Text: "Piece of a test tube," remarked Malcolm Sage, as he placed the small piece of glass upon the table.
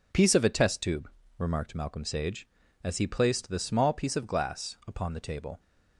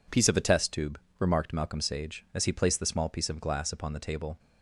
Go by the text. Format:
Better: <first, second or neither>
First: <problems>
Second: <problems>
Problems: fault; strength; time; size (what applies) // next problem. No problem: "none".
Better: neither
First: none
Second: none